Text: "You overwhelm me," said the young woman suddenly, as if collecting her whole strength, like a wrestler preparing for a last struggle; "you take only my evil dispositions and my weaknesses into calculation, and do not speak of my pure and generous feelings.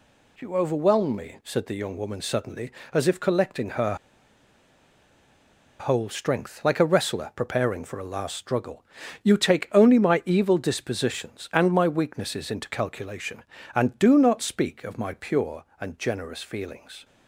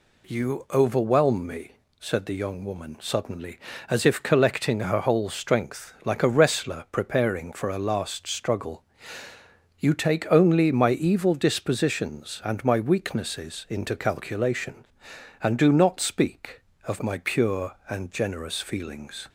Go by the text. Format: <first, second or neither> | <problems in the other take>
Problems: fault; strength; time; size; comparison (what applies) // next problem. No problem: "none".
second | pauses between "her" and "whole"; strong; at 3.9 s; 1.8 s long